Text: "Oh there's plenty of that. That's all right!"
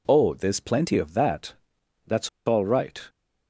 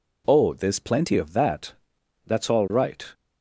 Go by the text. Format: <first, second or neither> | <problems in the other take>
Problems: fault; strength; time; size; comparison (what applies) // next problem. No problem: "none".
second | pauses between "That's" and "all"; slight; at 2.2 s; 0.17 s long